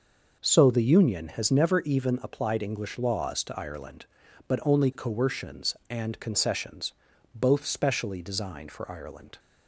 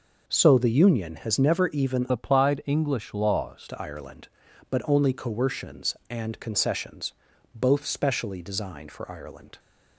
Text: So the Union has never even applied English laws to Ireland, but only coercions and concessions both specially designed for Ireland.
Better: first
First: pauses between "concessions" and "both"; at 6.9 s; 0.40 s long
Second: changes voice from "applied" to "laws"; from 2.0 to 3.6 s; 1.6 s long // pauses between "concessions" and "both"; at 7.1 s; 0.40 s long

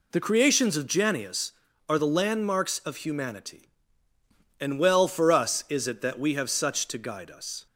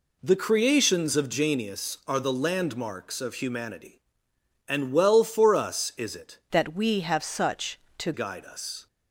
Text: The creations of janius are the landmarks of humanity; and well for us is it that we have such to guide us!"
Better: first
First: none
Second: changes voice from "that" to "to"; from 6.5 to 8.1 s; 1.6 s long

